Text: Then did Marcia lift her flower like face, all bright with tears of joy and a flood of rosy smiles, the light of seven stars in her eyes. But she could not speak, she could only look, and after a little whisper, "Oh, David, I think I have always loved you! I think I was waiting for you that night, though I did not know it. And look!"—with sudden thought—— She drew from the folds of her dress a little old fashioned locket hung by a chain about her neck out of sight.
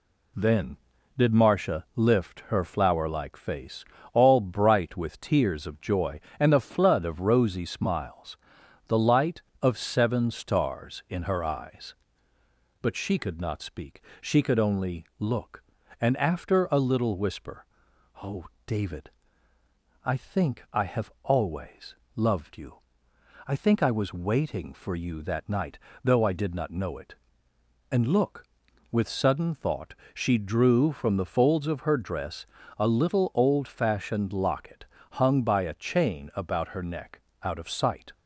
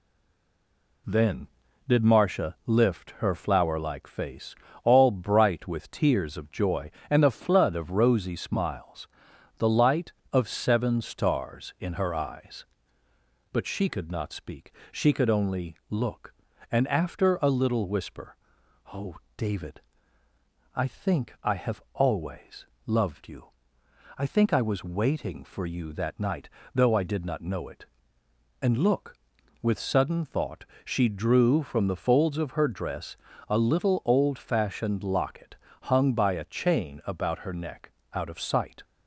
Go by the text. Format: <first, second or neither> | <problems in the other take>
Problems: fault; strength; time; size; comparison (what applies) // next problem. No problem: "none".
first | stays silent before the first word; until 1.0 s; 1.0 s long // pauses between "always" and "loved"; slight; at 22.6 s; 0.20 s long; slight in the first // pauses between "dress" and "a"; slight; at 33.1 s; 0.34 s long; slight in the first // pauses between "locket" and "hung"; slight; at 35.5 s; 0.28 s long; slight in the first // pauses between "neck" and "out"; slight; at 37.9 s; 0.22 s long; slight in the first